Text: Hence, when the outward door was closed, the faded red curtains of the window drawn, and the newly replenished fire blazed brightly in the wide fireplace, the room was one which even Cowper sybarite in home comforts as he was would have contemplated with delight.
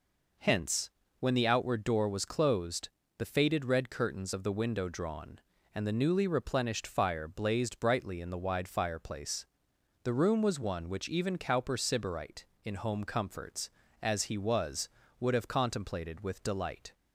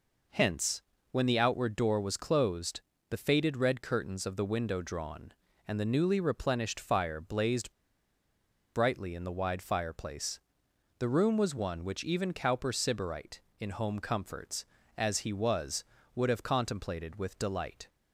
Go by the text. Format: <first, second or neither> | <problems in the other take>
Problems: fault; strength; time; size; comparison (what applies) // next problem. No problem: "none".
first | pauses between "blazed" and "brightly"; at 7.7 s; 1.0 s long